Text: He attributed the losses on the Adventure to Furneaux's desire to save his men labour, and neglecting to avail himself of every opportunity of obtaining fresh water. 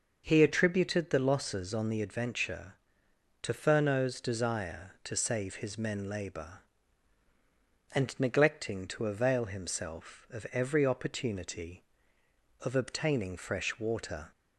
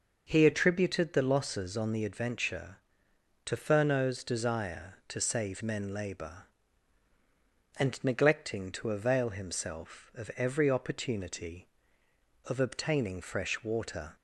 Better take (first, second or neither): first